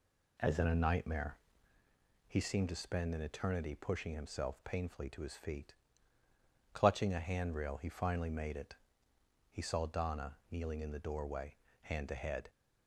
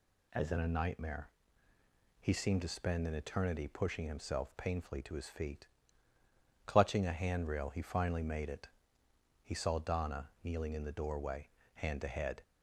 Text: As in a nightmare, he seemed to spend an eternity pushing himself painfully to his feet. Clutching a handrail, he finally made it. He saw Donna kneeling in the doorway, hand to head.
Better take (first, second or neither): second